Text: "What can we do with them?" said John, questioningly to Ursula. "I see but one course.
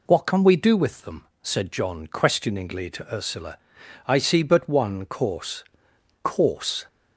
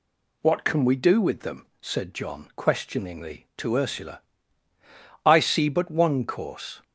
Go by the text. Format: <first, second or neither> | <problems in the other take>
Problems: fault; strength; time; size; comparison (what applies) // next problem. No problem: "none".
second | says "course" twice; at 6.2 s